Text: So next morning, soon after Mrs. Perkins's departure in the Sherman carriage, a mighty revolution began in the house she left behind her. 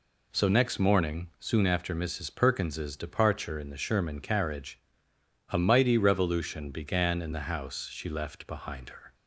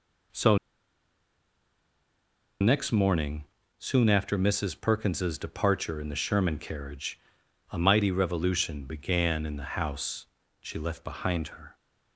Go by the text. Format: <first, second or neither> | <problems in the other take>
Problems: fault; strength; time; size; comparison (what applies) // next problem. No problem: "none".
first | pauses between "So" and "next"; strong; at 0.5 s; 2.0 s long // pauses between "house" and "she"; slight; at 10.2 s; 0.34 s long